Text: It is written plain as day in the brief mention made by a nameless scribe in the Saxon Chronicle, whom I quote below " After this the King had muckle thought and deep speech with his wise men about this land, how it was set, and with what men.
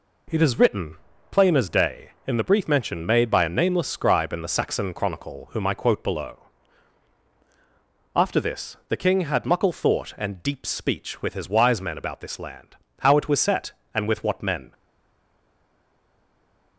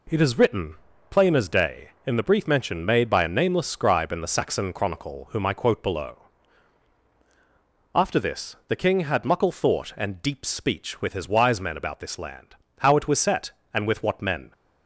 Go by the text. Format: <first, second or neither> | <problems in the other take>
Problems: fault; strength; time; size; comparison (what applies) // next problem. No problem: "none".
second | pauses between "written" and "plain"; slight; at 0.9 s; 0.34 s long; slight in the second // stays silent after the last word; noticeable; from 14.7 s on; 2.0 s long